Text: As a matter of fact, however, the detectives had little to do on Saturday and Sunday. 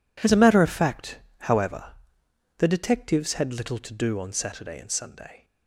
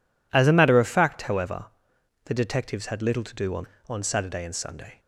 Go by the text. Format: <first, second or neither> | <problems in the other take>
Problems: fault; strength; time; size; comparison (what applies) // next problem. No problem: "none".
first | says "on" twice; at 3.8 s